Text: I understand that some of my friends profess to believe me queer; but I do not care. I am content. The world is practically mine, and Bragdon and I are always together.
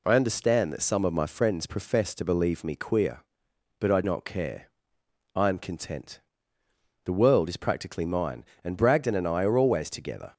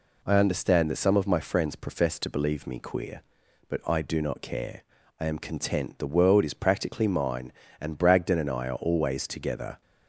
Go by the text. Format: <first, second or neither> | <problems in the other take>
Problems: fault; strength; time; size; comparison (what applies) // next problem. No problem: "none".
second | skips "do"; at 4.0 s